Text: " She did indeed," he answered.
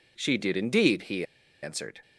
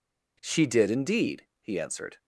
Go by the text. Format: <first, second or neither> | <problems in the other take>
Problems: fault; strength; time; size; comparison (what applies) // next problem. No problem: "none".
second | pauses between "he" and "answered"; at 1.2 s; 0.37 s long